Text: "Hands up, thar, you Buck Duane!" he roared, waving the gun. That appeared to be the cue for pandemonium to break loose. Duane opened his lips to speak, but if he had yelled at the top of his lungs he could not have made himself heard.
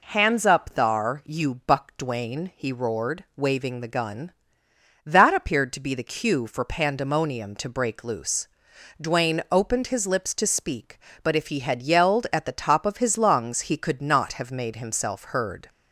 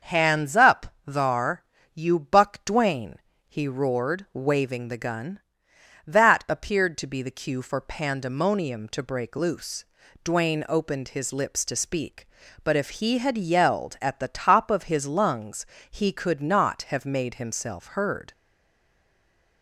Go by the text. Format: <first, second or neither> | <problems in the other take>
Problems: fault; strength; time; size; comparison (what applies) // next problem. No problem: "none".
first | starts louder than the rest; until 1.1 s; 6.5 dB // pauses between "lungs" and "he"; slight; at 15.6 s; 0.24 s long // stays silent after the last word; noticeable; from 18.3 s on; 1.3 s long